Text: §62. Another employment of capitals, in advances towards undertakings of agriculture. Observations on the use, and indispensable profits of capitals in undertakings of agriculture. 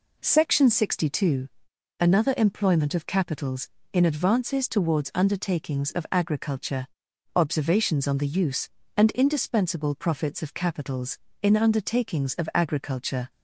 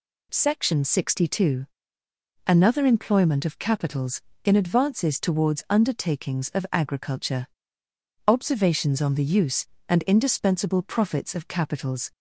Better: first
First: none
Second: stops before "in undertakings of agriculture"; at 12.1 s

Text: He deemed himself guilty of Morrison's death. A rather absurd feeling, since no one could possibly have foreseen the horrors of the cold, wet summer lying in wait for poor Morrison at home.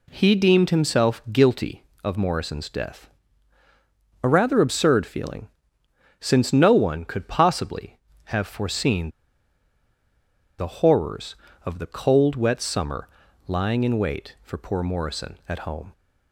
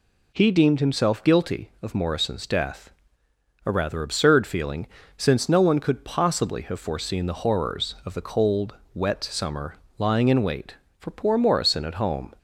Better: second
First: pauses between "foreseen" and "the"; strong; at 9.1 s; 1.4 s long // pauses between "summer" and "lying"; at 13.0 s; 0.40 s long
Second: pauses between "summer" and "lying"; slight; at 9.7 s; 0.22 s long

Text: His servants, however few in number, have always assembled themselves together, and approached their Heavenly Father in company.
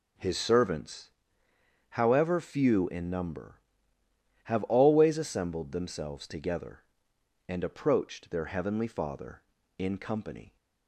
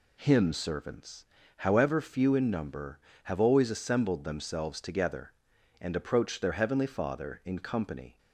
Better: first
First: none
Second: says "Him" for "His"; at 0.1 s

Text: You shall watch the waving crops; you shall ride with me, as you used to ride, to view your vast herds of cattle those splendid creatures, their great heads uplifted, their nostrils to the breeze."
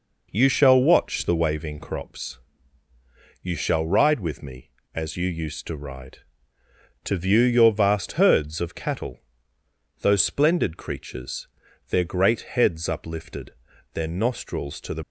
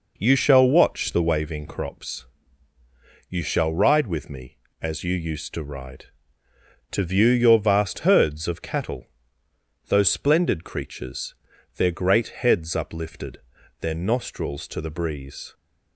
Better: second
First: pauses between "cattle" and "those"; noticeable; at 9.2 s; 0.82 s long // stops before "breeze"; at 15.0 s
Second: pauses between "cattle" and "those"; noticeable; at 9.0 s; 0.82 s long

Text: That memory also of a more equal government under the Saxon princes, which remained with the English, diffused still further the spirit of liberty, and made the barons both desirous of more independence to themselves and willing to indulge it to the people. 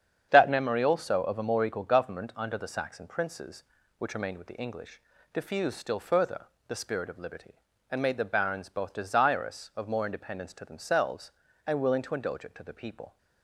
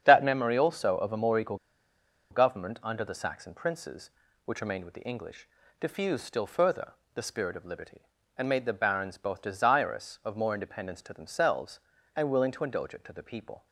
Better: first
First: starts louder than the rest; strong; until 1.3 s; 8 dB // pauses between "further" and "the"; slight; at 6.4 s; 0.22 s long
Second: starts louder than the rest; strong; until 1.0 s; 8 dB // pauses between "equal" and "government"; noticeable; at 1.5 s; 0.74 s long // pauses between "further" and "the"; slight; at 6.9 s; 0.22 s long

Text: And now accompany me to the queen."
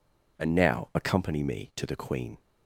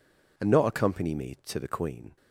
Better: first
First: none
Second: says "not" for "now"; at 0.4 s

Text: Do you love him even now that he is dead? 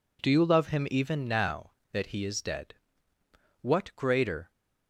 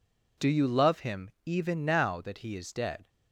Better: second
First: goes on to say "What greater"; noticeable; from 3.6 s on; 0.88 s long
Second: none

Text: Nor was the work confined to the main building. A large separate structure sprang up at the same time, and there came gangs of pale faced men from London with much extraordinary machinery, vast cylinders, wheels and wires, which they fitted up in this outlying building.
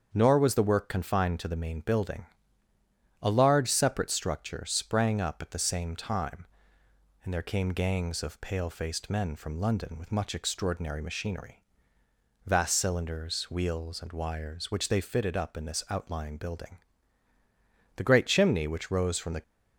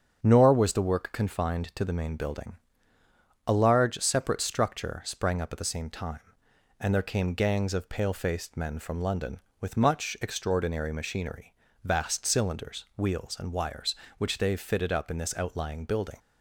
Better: second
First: starts louder than the rest; until 1.1 s; 7 dB // goes on to say "The great chimney which rose from the"; from 17.9 s on; 1.4 s long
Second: starts louder than the rest; strong; until 1.2 s; 7.5 dB

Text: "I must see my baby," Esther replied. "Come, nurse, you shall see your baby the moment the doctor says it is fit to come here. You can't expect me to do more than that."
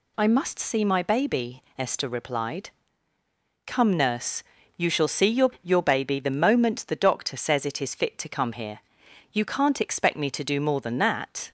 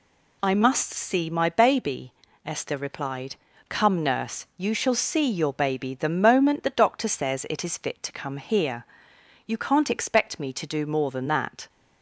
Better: second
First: says "your" twice; at 5.6 s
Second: none

